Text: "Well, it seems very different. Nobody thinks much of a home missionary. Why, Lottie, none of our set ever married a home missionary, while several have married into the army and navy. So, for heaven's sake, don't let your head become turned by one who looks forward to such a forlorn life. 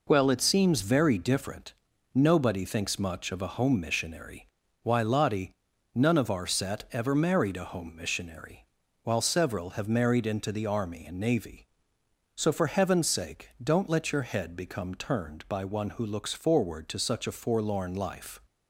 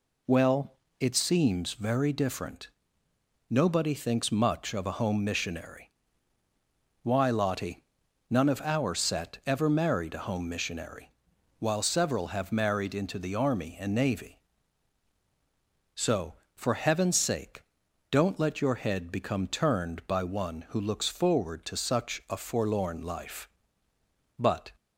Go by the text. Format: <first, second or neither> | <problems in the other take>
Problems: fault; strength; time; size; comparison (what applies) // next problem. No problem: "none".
first | goes on to say "But"; slight; from 24.3 s on; 0.34 s long